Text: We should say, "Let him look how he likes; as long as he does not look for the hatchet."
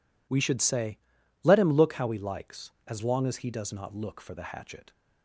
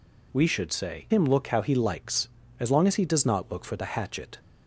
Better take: first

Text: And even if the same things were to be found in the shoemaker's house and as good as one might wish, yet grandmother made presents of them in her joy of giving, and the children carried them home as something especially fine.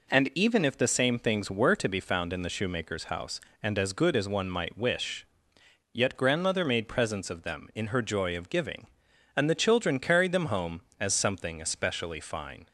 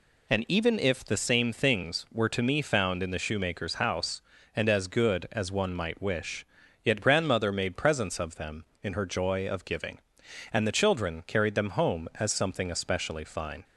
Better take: first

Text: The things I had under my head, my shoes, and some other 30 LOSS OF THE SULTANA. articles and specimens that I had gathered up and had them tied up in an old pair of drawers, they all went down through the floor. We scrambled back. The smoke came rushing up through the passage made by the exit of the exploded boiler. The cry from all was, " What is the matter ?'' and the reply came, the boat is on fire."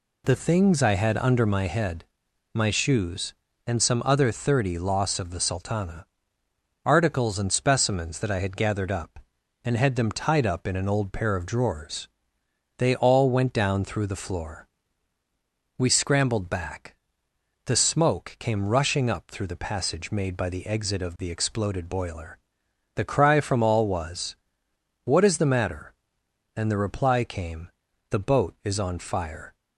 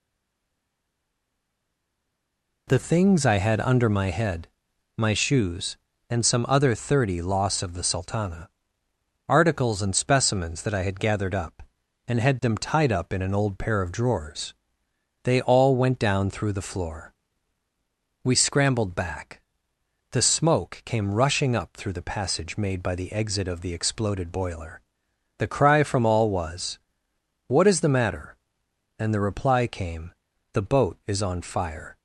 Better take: first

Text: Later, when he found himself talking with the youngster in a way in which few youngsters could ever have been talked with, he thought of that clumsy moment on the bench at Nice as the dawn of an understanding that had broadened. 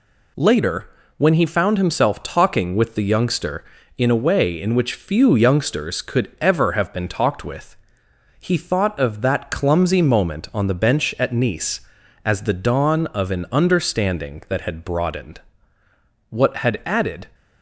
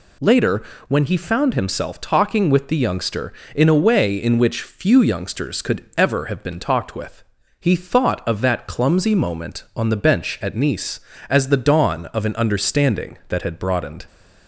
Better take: second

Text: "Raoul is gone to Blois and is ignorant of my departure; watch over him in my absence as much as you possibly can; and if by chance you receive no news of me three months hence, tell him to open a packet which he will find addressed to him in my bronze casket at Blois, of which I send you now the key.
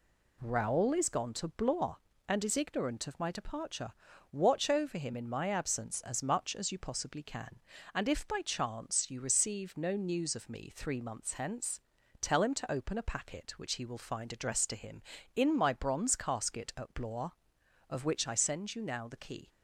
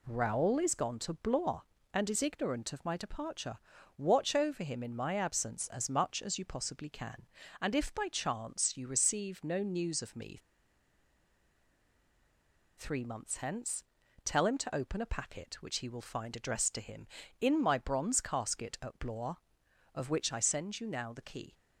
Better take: first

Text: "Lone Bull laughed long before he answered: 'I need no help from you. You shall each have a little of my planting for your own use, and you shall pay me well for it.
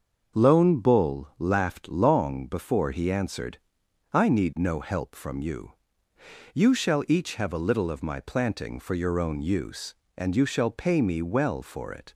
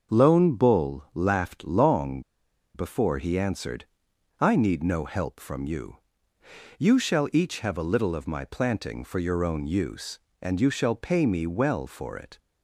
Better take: first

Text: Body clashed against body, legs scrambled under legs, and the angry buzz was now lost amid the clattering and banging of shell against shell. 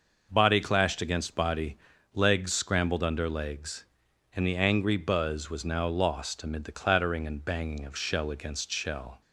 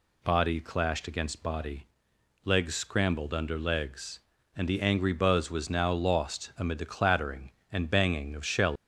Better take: first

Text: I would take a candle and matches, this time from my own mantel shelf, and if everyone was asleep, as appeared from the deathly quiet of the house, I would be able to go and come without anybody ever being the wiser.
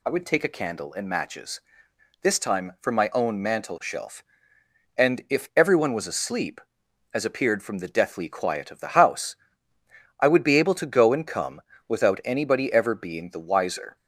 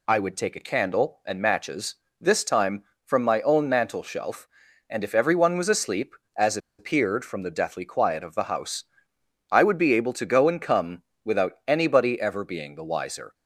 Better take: first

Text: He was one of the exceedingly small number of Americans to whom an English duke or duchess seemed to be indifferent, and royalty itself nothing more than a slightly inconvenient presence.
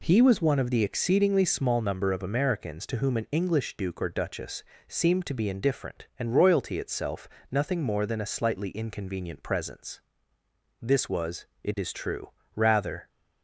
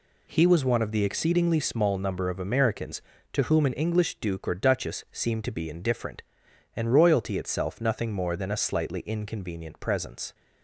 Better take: second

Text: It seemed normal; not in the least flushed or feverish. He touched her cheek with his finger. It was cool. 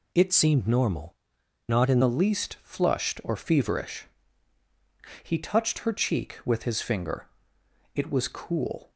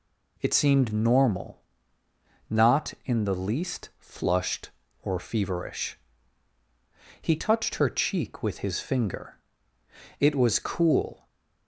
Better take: second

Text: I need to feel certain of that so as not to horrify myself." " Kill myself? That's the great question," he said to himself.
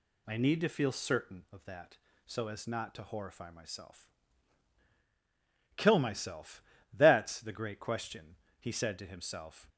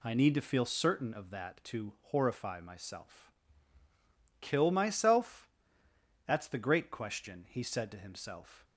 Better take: first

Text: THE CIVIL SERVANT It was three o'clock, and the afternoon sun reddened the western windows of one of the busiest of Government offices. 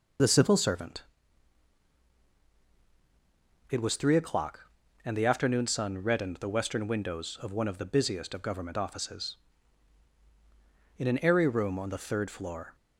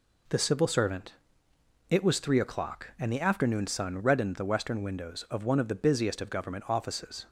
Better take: second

